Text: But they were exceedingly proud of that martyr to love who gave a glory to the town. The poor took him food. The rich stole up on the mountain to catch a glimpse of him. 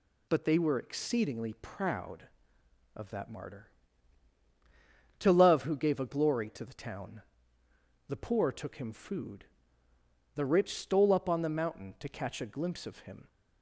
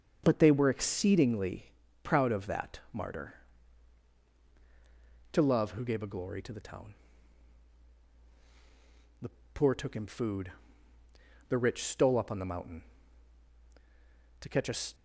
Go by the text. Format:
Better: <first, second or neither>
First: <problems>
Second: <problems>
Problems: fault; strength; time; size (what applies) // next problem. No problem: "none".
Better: first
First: none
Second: starts louder than the rest; until 1.2 s; 6.5 dB // pauses between "exceedingly" and "proud"; slight; at 1.6 s; 0.36 s long // pauses between "The" and "poor"; slight; at 9.2 s; 0.24 s long // stops before "glimpse of him"; at 14.9 s